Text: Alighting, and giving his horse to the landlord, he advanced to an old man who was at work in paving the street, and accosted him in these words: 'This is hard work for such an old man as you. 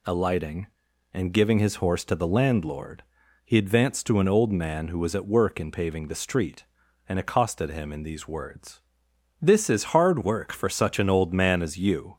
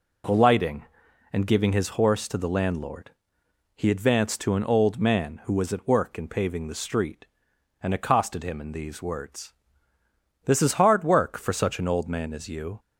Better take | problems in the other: neither | none

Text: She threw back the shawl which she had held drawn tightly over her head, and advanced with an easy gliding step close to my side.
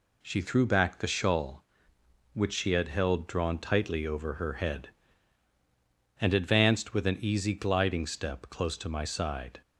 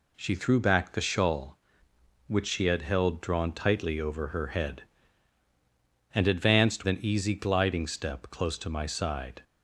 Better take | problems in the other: first | skips "with"; at 6.8 s

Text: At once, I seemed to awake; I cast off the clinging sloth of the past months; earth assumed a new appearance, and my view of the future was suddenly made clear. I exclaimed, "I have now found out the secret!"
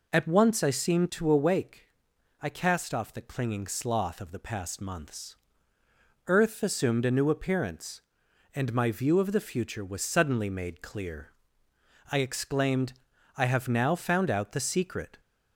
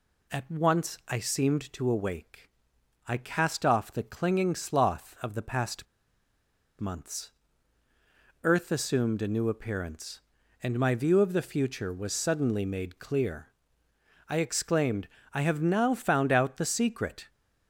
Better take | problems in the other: first | pauses between "past" and "months"; noticeable; at 5.8 s; 0.94 s long

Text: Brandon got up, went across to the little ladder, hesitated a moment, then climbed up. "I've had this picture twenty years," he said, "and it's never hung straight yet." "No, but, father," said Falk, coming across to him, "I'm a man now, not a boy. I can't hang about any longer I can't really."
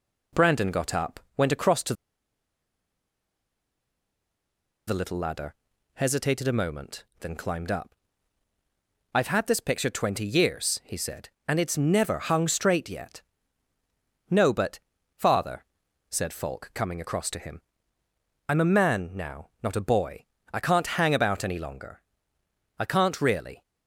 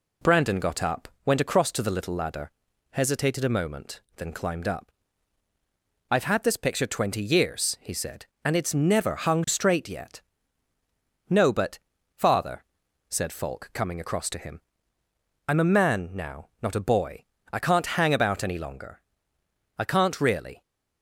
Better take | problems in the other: second | pauses between "to" and "the"; strong; at 1.9 s; 2.9 s long // pauses between "longer" and "I"; noticeable; at 22.0 s; 0.76 s long; noticeable in the second

